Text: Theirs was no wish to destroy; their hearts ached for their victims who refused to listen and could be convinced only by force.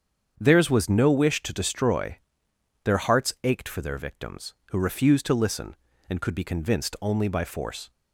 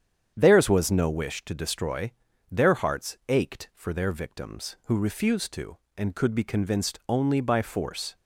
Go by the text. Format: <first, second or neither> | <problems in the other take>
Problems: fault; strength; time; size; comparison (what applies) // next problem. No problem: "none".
first | starts louder than the rest; strong; until 1.3 s; 8.5 dB; strong in the first // skips "listen"; at 5.8 s